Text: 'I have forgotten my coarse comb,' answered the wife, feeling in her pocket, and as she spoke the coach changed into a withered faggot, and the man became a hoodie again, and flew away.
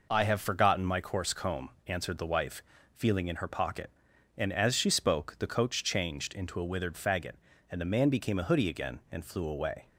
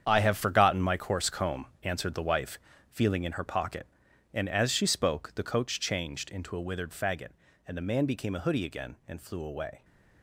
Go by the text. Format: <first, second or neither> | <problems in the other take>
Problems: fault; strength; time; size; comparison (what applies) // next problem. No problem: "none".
first | gets quieter; strong; throughout; 11.5 dB